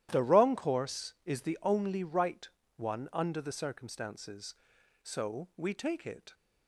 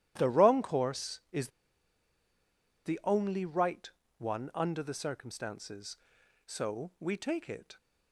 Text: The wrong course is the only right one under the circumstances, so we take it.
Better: first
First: starts louder than the rest; strong; until 1.1 s; 12.5 dB // pauses between "right" and "one"; slight; at 2.4 s; 0.30 s long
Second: starts louder than the rest; strong; until 1.1 s; 12.5 dB // pauses between "is" and "the"; strong; at 1.4 s; 1.3 s long // pauses between "right" and "one"; slight; at 3.8 s; 0.30 s long

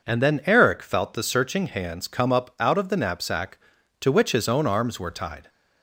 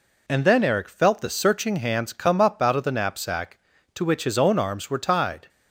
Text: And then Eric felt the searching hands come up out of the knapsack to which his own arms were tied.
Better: neither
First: none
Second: none

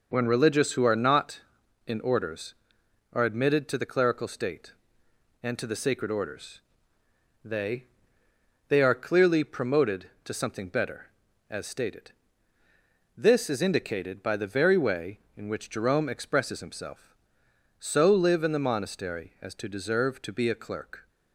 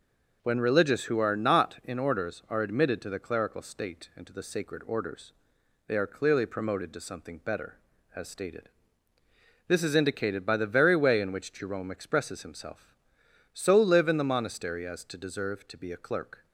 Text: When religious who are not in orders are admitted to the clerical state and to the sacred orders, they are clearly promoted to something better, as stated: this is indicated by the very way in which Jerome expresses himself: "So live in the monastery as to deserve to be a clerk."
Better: second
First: says "they" twice; at 8.6 s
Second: none

